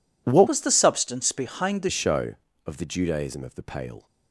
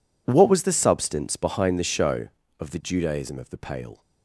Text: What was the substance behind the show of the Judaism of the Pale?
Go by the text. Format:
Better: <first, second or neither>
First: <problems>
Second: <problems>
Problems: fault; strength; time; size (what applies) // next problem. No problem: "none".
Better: second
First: changes voice from "was" to "the"; from 0.4 to 1.8 s; 1.4 s long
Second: none